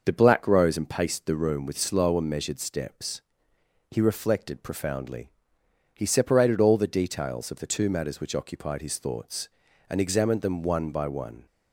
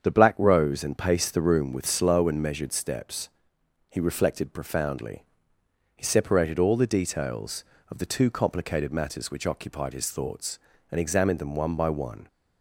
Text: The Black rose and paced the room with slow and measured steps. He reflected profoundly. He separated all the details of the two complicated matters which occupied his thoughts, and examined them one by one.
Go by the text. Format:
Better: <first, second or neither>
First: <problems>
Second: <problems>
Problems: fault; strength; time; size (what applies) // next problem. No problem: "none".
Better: second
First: starts louder than the rest; noticeable; until 1.0 s; 6 dB // skips "complicated"; at 7.8 s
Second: starts louder than the rest; strong; until 1.0 s; 7.5 dB